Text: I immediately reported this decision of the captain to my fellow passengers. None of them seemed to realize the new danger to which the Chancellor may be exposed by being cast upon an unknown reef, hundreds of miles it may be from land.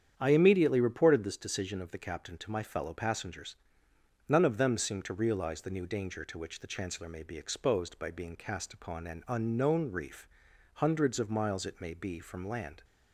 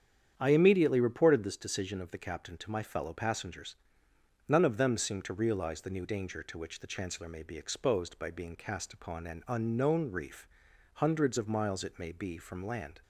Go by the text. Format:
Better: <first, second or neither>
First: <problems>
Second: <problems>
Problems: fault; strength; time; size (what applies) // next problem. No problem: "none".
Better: neither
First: starts louder than the rest; strong; until 1.1 s; 8.5 dB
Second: starts louder than the rest; strong; until 1.3 s; 8.5 dB